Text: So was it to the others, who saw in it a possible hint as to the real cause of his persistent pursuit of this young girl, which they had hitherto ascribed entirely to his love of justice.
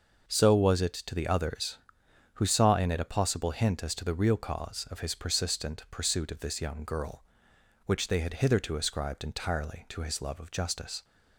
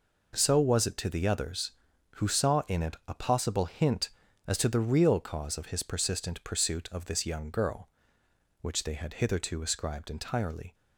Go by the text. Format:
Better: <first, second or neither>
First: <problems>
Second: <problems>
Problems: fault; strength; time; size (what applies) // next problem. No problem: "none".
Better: first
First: none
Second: stops before "to his love of justice"; at 10.7 s